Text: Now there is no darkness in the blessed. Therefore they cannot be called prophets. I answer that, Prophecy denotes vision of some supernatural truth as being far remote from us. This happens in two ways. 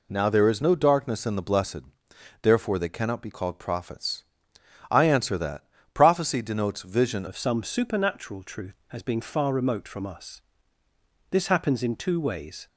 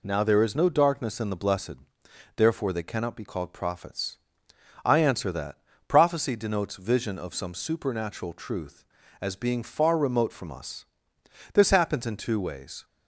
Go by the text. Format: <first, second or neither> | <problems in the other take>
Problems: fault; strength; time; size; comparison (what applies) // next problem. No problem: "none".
second | changes voice at "of"; from 7.2 s on; 5.4 s long